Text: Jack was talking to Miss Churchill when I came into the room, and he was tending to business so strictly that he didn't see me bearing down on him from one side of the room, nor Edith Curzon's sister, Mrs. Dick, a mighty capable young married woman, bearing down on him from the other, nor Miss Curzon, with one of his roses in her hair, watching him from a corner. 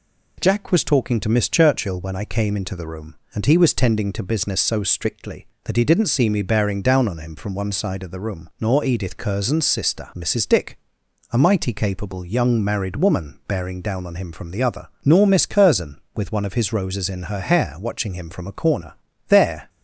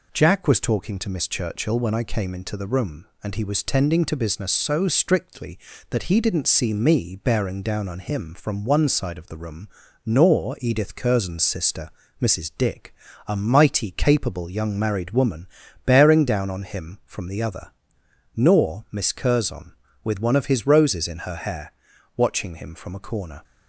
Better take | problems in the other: second | goes on to say "There"; slight; from 19.2 s on; 0.42 s long

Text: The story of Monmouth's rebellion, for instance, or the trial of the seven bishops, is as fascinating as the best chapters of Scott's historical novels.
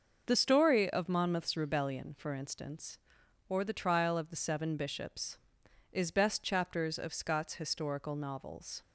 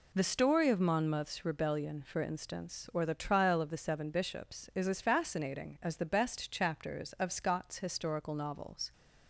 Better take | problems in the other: second | starts louder than the rest; noticeable; until 1.2 s; 6 dB // skips "as fascinating as the"; at 6.0 s

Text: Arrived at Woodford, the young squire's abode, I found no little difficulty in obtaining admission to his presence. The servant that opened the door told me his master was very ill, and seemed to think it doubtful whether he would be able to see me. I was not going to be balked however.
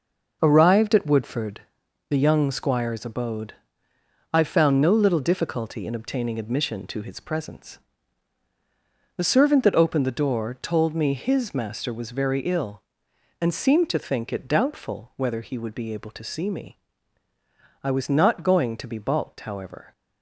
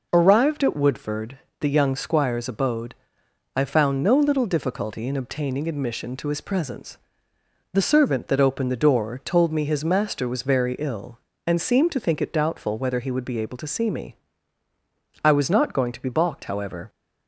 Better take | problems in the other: neither | none

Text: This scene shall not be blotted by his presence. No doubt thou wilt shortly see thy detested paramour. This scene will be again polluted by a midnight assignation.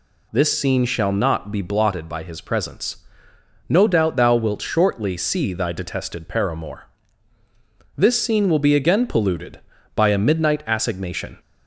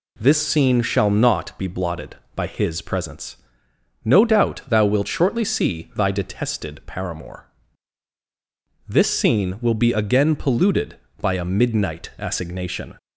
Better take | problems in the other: neither | none

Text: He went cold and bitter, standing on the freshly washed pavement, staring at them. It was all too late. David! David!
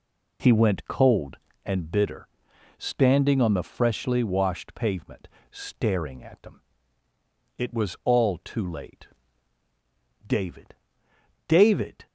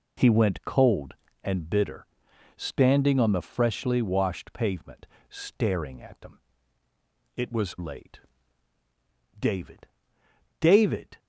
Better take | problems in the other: first | skips "all too"; at 7.7 s

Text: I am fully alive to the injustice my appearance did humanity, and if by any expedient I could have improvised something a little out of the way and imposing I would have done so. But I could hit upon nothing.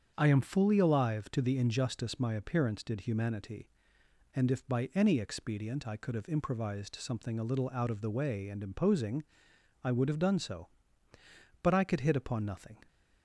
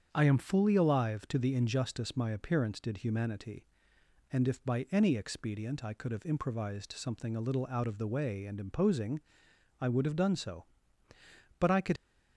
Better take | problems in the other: first | starts louder than the rest; strong; until 1.1 s; 7.5 dB; strong in the first // pauses between "imposing" and "I"; noticeable; at 9.1 s; 0.60 s long; noticeable in the first // stops before "hit upon nothing"; at 11.9 s

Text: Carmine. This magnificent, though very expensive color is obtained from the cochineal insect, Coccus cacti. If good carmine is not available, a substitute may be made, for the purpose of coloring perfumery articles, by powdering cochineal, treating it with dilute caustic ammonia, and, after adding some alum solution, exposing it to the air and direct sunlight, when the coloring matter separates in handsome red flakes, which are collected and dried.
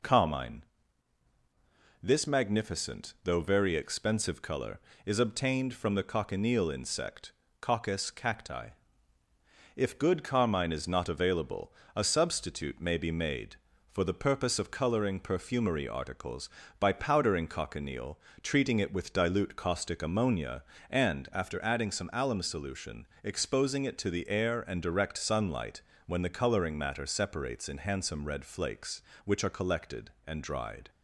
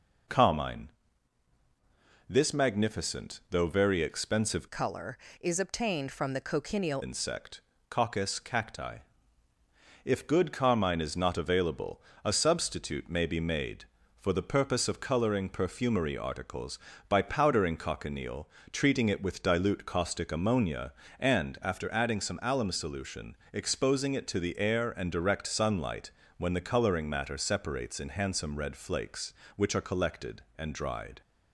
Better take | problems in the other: first | changes voice from "color" to "cochineal"; from 4.6 to 7.0 s; 2.4 s long

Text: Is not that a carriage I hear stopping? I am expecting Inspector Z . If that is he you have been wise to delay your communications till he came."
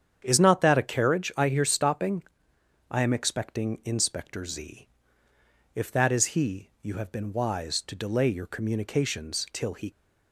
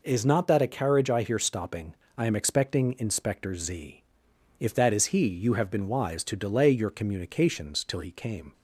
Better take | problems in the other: second | starts louder than the rest; strong; until 1.2 s; 8 dB // stops before "came"; at 9.9 s

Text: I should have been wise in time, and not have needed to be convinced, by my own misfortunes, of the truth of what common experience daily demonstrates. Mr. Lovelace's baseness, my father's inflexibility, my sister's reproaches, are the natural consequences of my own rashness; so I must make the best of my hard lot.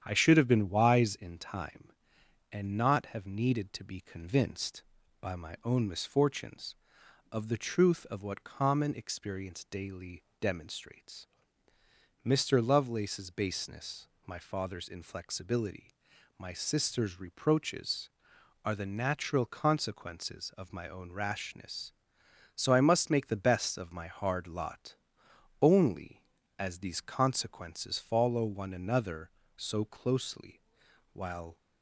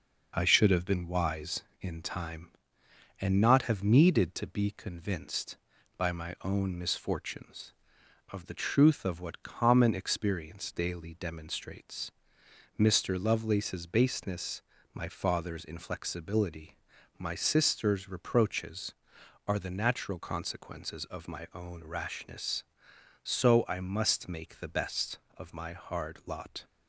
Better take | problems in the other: second | starts louder than the rest; strong; until 1.0 s; 9 dB // pauses between "daily" and "demonstrates"; slight; at 10.2 s; 0.18 s long // goes on to say "Only as these consequences follow one another so closely while"; strong; from 25.6 s on; 5.9 s long

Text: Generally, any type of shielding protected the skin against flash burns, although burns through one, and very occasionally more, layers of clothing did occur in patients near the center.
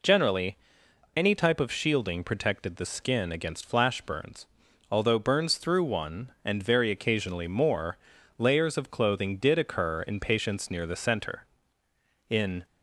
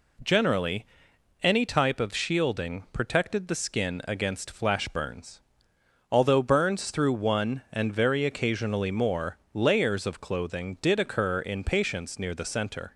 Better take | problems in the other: second | goes on to say "In"; slight; from 12.2 s on; 0.36 s long

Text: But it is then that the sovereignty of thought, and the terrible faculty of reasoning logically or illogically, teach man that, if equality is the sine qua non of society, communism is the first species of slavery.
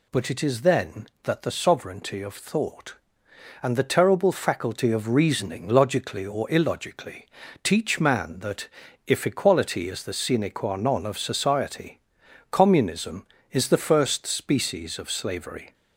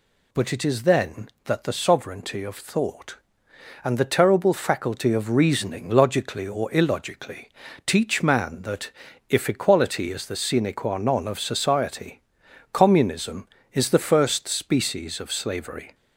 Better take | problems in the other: neither | none

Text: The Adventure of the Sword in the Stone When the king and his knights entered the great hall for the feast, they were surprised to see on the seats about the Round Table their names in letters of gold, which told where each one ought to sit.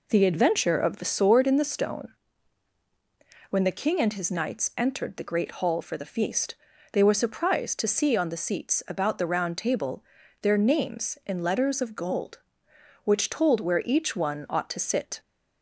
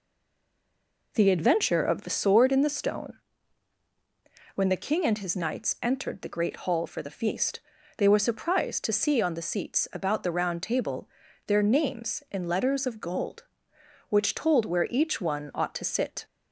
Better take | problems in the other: first | stays silent before the first word; until 1.1 s; 1.1 s long // pauses between "Stone" and "When"; strong; at 3.1 s; 1.3 s long; strong in the first // pauses between "Table" and "their"; at 11.0 s; 0.38 s long; also in the first

